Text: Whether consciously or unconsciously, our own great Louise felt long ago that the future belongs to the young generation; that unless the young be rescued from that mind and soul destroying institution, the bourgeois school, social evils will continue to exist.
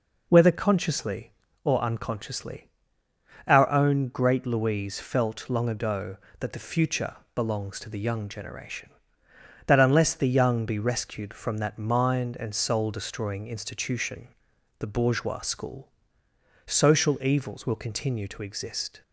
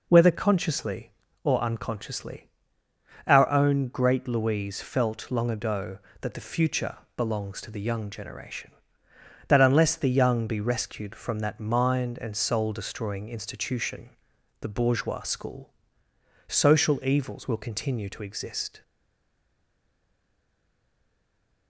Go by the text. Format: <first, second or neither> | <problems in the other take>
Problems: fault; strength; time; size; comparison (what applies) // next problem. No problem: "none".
first | pauses between "future" and "belongs"; slight; at 6.9 s; 0.22 s long; slight in the first // stays silent after the last word; strong; from 18.8 s on; 2.8 s long